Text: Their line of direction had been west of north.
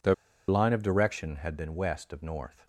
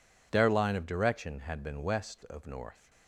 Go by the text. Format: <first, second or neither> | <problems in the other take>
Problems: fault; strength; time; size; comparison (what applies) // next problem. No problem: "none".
second | pauses between "Their" and "line"; slight; at 0.1 s; 0.33 s long